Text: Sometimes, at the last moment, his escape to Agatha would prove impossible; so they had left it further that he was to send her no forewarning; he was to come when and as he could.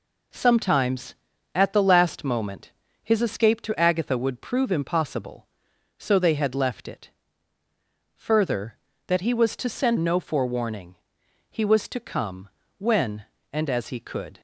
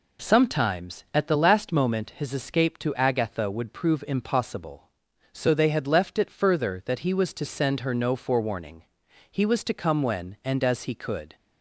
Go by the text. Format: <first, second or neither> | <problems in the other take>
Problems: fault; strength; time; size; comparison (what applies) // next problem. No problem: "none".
second | pauses between "it" and "further"; at 7.0 s; 1.0 s long // skips "her"; at 9.9 s // pauses between "come" and "when"; slight; at 12.4 s; 0.30 s long